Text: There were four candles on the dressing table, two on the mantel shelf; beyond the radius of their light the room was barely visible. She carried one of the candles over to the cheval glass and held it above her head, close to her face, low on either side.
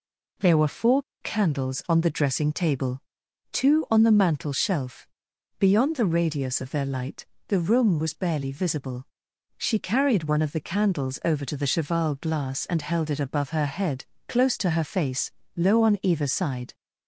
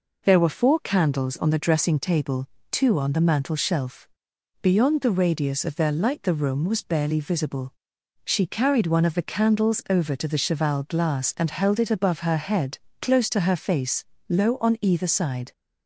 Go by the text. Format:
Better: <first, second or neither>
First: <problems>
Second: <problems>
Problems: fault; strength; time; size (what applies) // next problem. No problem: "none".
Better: second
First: pauses between "four" and "candles"; slight; at 1.0 s; 0.20 s long // pauses between "light" and "the"; slight; at 7.2 s; 0.24 s long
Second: none